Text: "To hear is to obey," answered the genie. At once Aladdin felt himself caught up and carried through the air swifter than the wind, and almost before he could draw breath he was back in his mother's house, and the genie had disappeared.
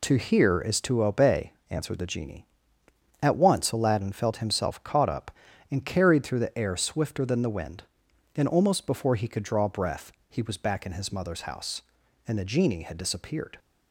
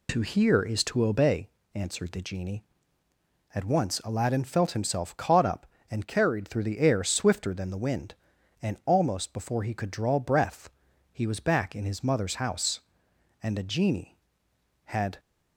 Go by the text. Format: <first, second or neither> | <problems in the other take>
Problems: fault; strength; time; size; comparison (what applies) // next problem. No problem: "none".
first | pauses between "breath" and "he"; at 10.6 s; 0.44 s long; slight in the first // stops before "disappeared"; at 15.1 s